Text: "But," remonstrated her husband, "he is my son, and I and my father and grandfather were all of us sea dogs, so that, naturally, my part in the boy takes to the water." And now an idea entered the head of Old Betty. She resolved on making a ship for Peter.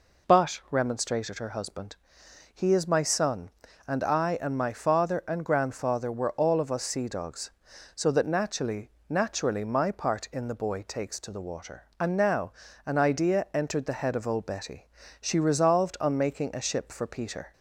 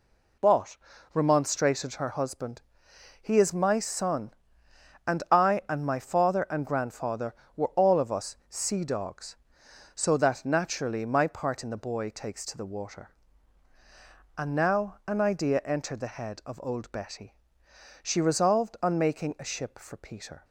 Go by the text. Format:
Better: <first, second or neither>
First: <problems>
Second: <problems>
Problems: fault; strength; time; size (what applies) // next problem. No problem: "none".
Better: second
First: says "naturally" twice; at 9.0 s // pauses between "now" and "an"; slight; at 12.5 s; 0.34 s long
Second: none